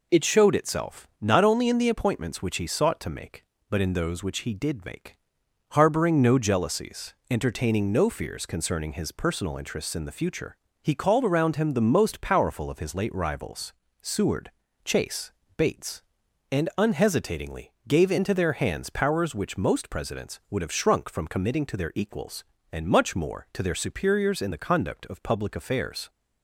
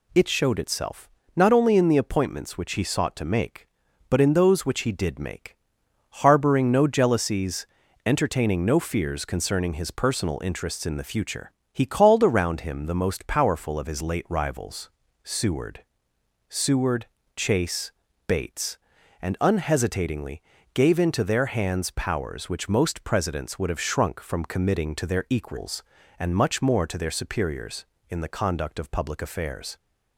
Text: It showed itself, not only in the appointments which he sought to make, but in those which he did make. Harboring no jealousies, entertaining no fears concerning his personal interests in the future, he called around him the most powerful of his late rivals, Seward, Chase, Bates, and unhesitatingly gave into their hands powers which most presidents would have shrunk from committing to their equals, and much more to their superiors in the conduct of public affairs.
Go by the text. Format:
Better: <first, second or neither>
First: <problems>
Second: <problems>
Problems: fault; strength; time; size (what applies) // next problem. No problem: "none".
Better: first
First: pauses between "unhesitatingly" and "gave"; slight; at 17.7 s; 0.16 s long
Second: says "Seward" twice; at 16.4 s // pauses between "unhesitatingly" and "gave"; slight; at 20.4 s; 0.32 s long